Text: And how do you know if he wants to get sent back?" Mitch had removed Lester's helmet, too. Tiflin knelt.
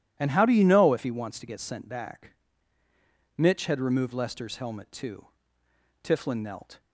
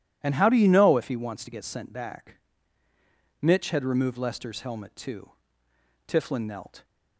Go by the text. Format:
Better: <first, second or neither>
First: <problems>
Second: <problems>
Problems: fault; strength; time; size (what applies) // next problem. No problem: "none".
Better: neither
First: none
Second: none